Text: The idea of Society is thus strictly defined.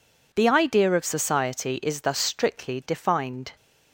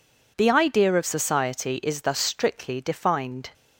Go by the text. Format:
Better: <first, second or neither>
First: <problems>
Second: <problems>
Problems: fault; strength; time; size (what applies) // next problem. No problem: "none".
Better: neither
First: none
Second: none